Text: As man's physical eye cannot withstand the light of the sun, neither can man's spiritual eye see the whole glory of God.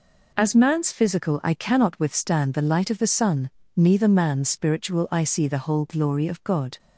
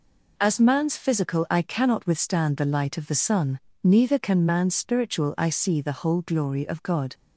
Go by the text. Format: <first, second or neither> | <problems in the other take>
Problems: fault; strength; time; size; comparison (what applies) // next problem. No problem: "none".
second | skips "can"; at 4.0 s